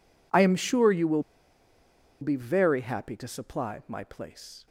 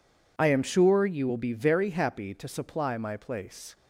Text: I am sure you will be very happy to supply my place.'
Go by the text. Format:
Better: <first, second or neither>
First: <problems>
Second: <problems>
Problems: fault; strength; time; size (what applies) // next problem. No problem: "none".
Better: second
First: pauses between "will" and "be"; at 1.2 s; 0.99 s long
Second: none